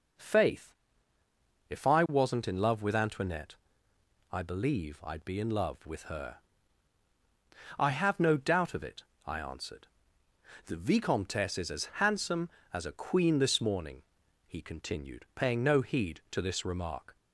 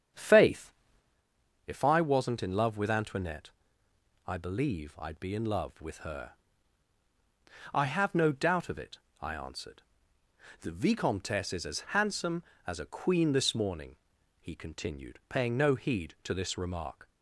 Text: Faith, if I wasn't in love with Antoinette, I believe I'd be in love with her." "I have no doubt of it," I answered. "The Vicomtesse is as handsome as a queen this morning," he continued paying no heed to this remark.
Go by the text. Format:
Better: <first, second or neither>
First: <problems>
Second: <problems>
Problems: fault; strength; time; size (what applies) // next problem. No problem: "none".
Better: first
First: none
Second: starts louder than the rest; strong; until 1.2 s; 8 dB